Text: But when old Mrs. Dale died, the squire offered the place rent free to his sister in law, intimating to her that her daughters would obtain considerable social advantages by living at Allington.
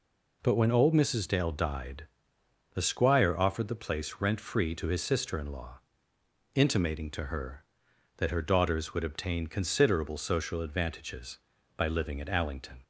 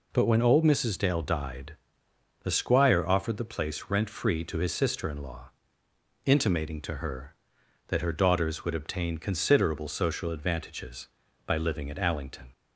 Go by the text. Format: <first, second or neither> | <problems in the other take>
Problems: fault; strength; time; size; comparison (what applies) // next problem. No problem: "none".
neither | none